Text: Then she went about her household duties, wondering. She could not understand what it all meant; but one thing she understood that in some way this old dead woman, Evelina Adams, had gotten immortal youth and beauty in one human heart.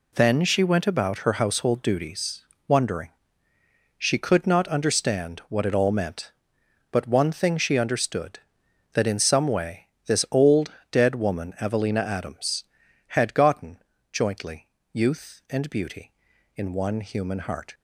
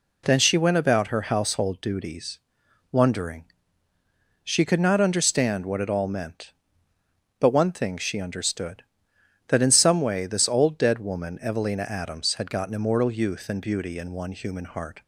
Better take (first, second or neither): second